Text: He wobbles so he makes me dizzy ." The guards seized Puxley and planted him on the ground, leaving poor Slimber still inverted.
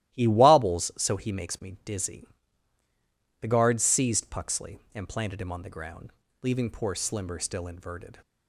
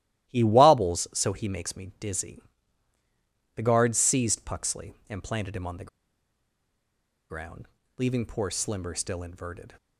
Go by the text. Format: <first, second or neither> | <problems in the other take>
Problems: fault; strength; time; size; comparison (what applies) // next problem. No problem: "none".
first | starts louder than the rest; strong; until 1.3 s; 12 dB; strong in the first // pauses between "the" and "ground"; strong; at 5.8 s; 1.4 s long